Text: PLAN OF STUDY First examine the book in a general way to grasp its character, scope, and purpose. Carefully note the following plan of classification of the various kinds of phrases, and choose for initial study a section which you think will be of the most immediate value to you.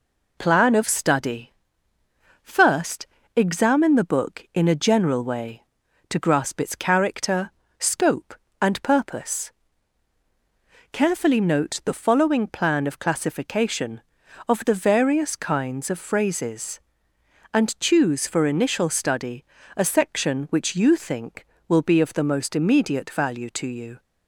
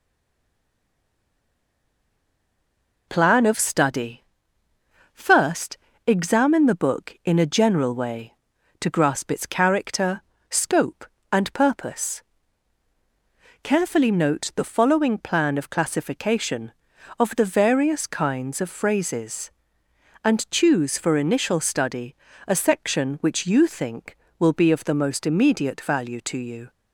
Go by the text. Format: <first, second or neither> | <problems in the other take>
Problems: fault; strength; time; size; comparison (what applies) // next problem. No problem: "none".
first | stays silent before the first word; strong; until 3.0 s; 3.0 s long // pauses between "STUDY" and "First"; noticeable; at 4.2 s; 0.88 s long; noticeable in the first // pauses between "First" and "examine"; slight; at 5.7 s; 0.26 s long; slight in the first // pauses between "study" and "a"; slight; at 22.1 s; 0.32 s long; slight in the first